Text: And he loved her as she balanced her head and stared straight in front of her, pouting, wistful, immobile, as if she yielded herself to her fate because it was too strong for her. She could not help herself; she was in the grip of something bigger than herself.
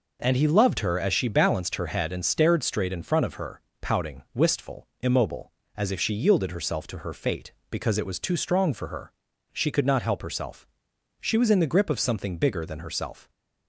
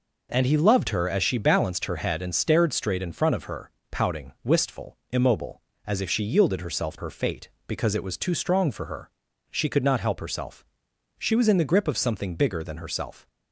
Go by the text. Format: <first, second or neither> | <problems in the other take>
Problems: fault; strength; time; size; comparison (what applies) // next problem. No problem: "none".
first | skips "to"; at 6.9 s